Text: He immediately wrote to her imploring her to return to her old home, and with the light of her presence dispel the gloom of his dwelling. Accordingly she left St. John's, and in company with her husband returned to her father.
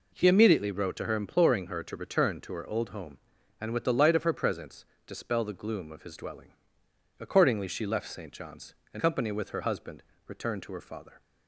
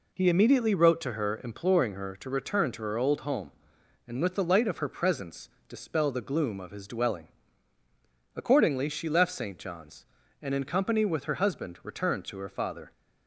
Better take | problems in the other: second | pauses between "presence" and "dispel"; slight; at 4.8 s; 0.22 s long; slight in the second // skips "in"; at 8.9 s // pauses between "husband" and "returned"; slight; at 10.0 s; 0.24 s long

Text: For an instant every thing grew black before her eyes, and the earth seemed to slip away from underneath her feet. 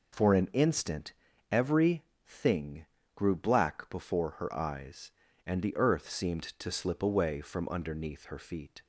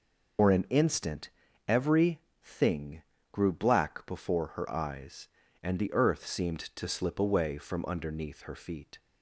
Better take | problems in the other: first | loses the start of "For"; at 0.3 s; 100 ms // pauses between "instant" and "every"; at 1.2 s; 0.38 s long; also in the first // pauses between "every" and "thing"; slight; at 2.2 s; 0.20 s long; slight in the first // pauses between "thing" and "grew"; slight; at 3.0 s; 0.30 s long; slight in the first

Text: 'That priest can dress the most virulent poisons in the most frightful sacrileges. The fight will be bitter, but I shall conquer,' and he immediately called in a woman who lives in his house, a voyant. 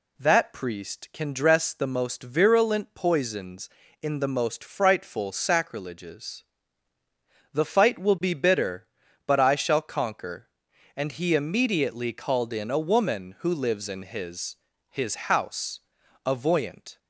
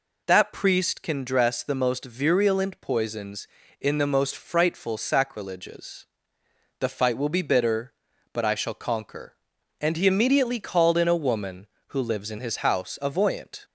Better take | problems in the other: second | says "his" twice; at 14.9 s

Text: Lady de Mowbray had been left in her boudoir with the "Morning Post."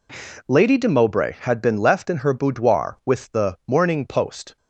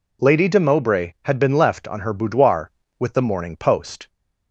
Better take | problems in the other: first | says "on" for "in"; at 1.8 s

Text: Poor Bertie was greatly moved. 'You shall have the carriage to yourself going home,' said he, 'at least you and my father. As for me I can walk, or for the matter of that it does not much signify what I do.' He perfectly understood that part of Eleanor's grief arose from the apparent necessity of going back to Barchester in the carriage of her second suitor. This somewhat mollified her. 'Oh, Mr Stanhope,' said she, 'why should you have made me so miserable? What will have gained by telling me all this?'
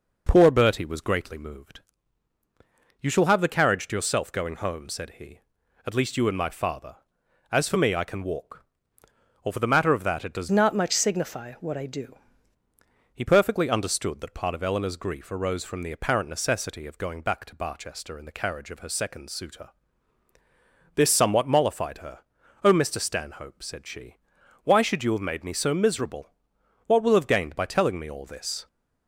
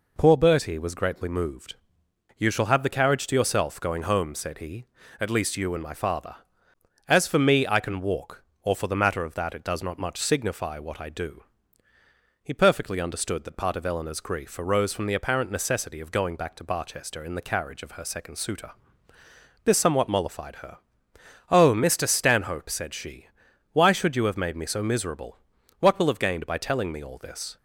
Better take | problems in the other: second | changes voice from "not" to "do"; from 10.4 to 12.1 s; 1.7 s long

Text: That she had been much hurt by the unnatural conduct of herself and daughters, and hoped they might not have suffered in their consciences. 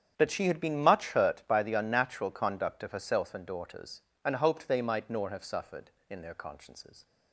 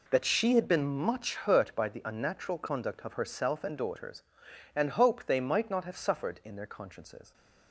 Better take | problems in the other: second | starts louder than the rest; strong; until 1.1 s; 8.5 dB // says "nor" for "not"; at 5.0 s

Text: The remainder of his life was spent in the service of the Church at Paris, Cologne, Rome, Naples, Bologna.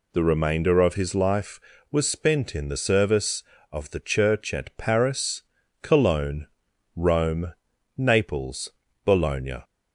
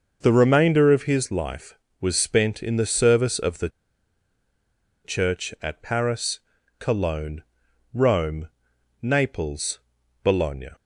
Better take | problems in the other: first | starts louder than the rest; noticeable; until 1.2 s; 6 dB // pauses between "the" and "Church"; strong; at 3.6 s; 1.3 s long

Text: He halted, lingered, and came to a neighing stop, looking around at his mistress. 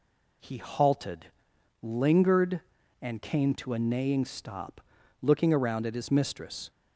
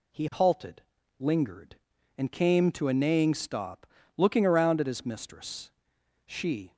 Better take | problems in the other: first | goes on to say "She"; from 6.2 s on; 0.50 s long

